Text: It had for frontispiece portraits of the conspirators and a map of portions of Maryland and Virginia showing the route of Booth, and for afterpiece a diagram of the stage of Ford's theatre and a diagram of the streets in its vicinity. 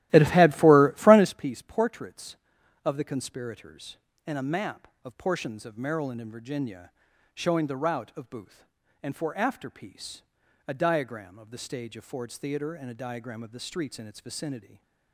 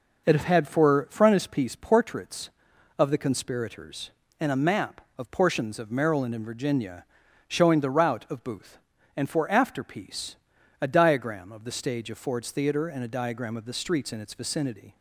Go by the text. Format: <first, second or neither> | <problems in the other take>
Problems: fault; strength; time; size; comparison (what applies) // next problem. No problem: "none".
second | starts louder than the rest; strong; until 1.4 s; 15 dB // pauses between "Virginia" and "showing"; noticeable; at 6.8 s; 0.46 s long; noticeable in the second // pauses between "afterpiece" and "a"; at 10.2 s; 0.44 s long; also in the second // stays silent after the last word; slight; from 14.5 s on; 0.6 s long